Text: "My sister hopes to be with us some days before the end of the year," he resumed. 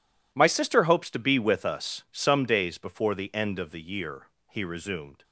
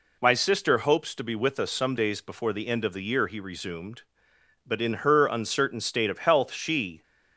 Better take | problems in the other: first | goes on to say "But in her uncertain state of health she"; strong; from 4.6 s on; 2.3 s long

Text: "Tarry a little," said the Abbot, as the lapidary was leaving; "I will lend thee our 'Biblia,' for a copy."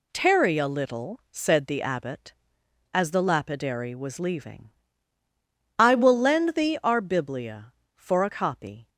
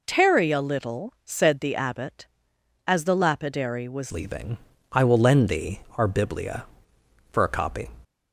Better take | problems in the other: first | changes voice at "leaving"; from 4.1 s on; 3.7 s long // pauses between "thee" and "our"; slight; at 5.8 s; 0.16 s long

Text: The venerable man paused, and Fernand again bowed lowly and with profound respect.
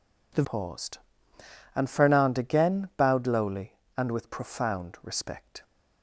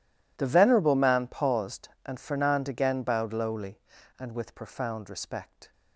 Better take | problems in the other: second | skips "venerable man"; at 0.4 s

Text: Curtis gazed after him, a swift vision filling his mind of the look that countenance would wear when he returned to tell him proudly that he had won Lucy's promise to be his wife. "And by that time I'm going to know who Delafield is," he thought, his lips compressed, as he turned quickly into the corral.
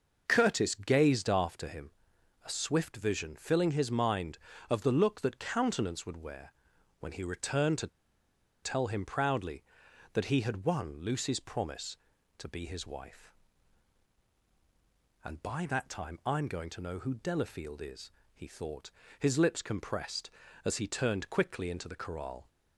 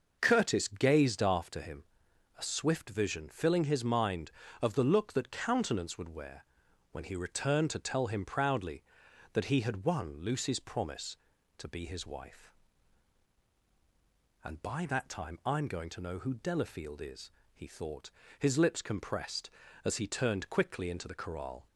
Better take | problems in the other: second | pauses between "wear" and "when"; noticeable; at 6.5 s; 0.48 s long; noticeable in the second // pauses between "to" and "tell"; noticeable; at 7.8 s; 0.74 s long

